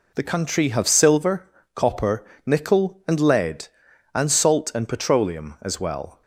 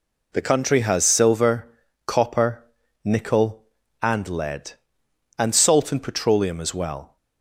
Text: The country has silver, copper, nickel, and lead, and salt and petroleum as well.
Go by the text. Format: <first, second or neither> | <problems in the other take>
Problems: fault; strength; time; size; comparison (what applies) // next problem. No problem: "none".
second | says "have" for "has"; at 0.6 s